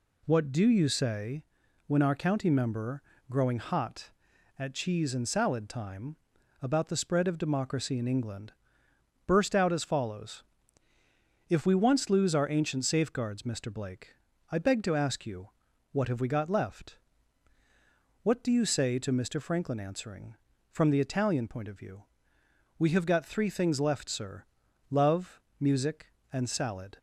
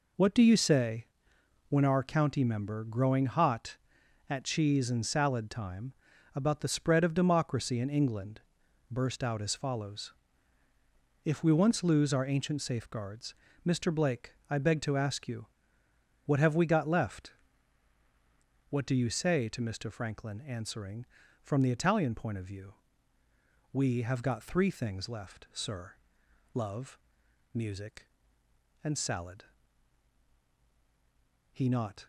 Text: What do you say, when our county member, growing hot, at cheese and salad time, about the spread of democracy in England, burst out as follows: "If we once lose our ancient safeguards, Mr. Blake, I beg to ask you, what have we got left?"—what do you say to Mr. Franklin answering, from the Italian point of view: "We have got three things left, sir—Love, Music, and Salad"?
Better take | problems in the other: first | goes on to say "He not"; from 31.5 s on; 0.52 s long

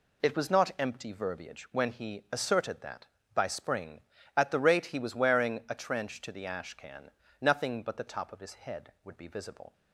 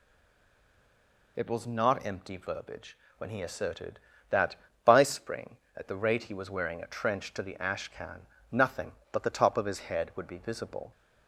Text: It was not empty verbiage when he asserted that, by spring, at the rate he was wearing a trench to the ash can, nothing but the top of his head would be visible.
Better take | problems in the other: first | stays silent before the first word; noticeable; until 1.3 s; 1.3 s long // pauses between "verbiage" and "when"; slight; at 2.9 s; 0.22 s long

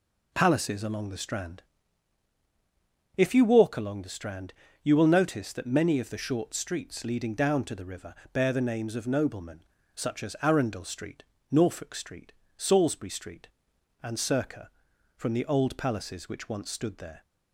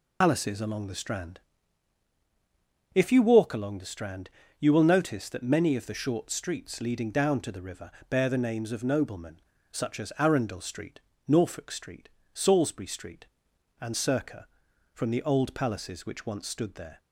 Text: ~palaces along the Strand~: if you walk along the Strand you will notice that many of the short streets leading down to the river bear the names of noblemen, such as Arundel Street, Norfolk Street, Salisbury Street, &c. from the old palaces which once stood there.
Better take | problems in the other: first | loses the start of "palaces"; at 0.2 s; 90 ms // pauses between "Strand" and "you"; slight; at 4.3 s; 0.28 s long; slight in the first // pauses between "river" and "bear"; slight; at 7.9 s; 0.18 s long; slight in the first

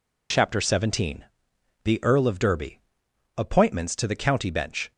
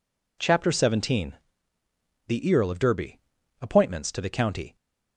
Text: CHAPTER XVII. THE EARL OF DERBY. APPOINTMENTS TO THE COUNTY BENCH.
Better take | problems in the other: first | stops before "BENCH"; at 4.7 s

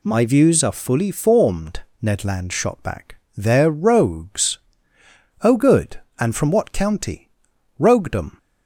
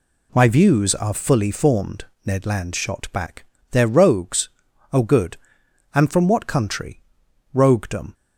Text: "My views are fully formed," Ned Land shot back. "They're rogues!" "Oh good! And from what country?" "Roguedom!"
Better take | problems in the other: second | says "county" for "country"; at 6.7 s

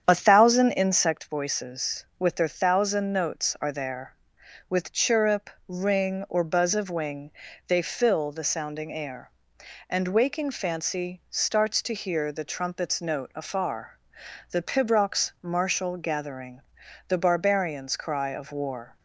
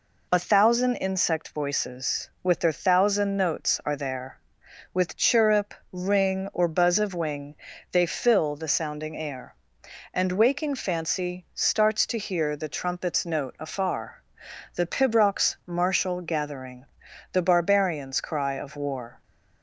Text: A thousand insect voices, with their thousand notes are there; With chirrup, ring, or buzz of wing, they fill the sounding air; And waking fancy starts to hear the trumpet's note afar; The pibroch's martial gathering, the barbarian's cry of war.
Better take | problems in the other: second | starts louder than the rest; strong; until 1.3 s; 8.5 dB

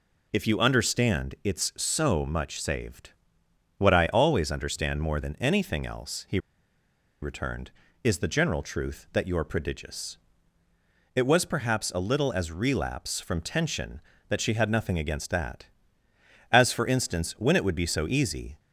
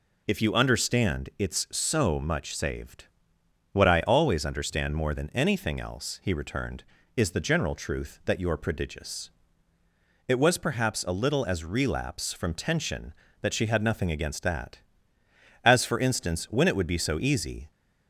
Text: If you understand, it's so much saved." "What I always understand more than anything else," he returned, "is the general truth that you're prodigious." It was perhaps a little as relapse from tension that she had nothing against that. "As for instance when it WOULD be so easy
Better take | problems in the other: second | pauses between "he" and "returned"; noticeable; at 6.3 s; 0.84 s long

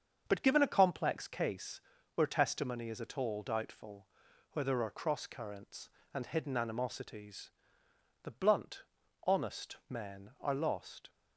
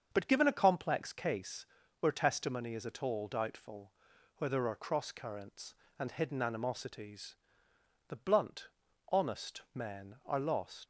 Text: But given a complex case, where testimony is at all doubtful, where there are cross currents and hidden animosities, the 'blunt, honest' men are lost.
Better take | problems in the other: first | starts louder than the rest; until 1.1 s; 7 dB; also in the first // leaves "lost" unfinished; at 10.8 s; 80 ms

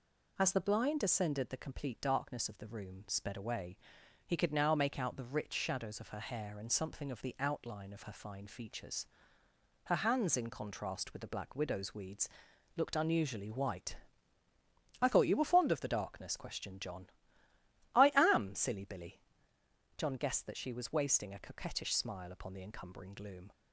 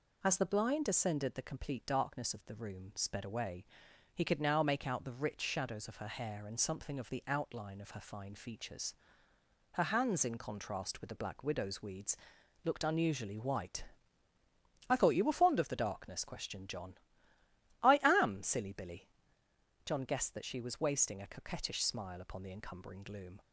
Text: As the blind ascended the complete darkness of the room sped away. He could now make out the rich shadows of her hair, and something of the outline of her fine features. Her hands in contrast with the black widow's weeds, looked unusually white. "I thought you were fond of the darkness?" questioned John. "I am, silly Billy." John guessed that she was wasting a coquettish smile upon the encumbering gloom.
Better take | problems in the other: neither | none

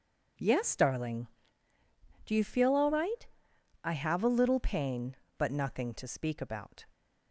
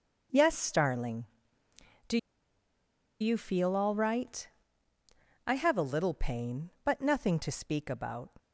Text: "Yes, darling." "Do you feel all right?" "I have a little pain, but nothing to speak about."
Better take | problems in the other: first | starts louder than the rest; until 2.1 s; 6.5 dB // pauses between "Do" and "you"; at 2.1 s; 1.0 s long

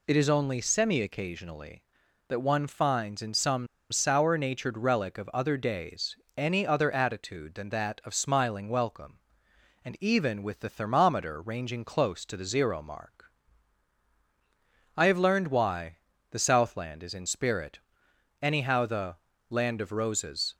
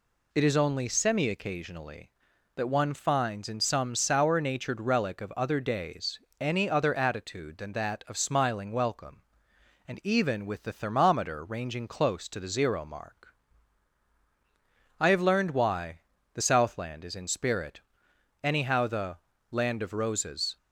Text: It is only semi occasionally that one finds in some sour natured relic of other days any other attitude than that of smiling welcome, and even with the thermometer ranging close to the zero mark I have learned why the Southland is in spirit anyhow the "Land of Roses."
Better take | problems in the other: second | pauses between "some" and "sour"; slight; at 3.6 s; 0.26 s long // pauses between "days" and "any"; slight; at 6.1 s; 0.18 s long; slight in the second // pauses between "mark" and "I"; strong; at 13.3 s; 1.6 s long; strong in the second // pauses between "why" and "the"; slight; at 15.9 s; 0.32 s long; slight in the second // pauses between "spirit" and "anyhow"; noticeable; at 17.7 s; 0.62 s long; noticeable in the second // pauses between "the" and "Land"; slight; at 19.1 s; 0.34 s long; slight in the second

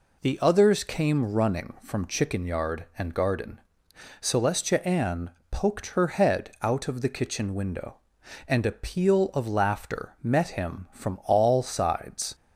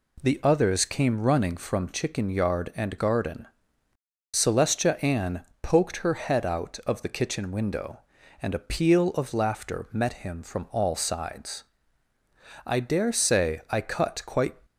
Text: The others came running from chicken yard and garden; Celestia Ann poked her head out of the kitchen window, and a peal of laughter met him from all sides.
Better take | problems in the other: first | pauses between "Ann" and "poked"; slight; at 5.4 s; 0.18 s long; slight in the first // goes on to say "I dare say I cut quite"; strong; from 12.6 s on; 1.9 s long

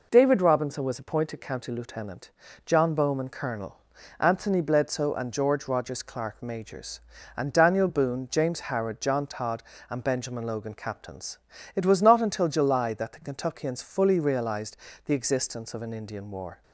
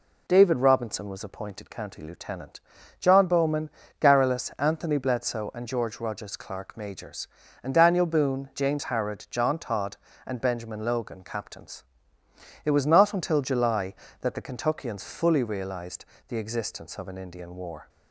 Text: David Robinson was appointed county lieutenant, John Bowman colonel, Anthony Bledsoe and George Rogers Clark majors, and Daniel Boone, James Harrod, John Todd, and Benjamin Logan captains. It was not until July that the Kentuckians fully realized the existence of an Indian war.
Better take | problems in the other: first | says "garrulus" for "colonel"; at 4.0 s // pauses between "realized" and "the"; slight; at 16.0 s; 0.24 s long; slight in the first

